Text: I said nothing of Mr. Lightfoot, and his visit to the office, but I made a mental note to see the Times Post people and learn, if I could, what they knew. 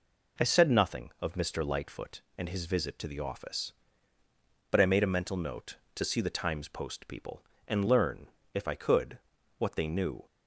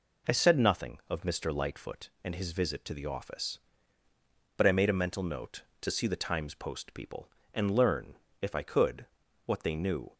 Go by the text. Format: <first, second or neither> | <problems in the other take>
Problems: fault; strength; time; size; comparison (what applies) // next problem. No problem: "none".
neither | none